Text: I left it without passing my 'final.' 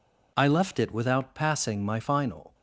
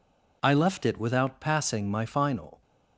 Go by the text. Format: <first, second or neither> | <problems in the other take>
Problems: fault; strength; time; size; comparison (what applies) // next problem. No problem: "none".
neither | none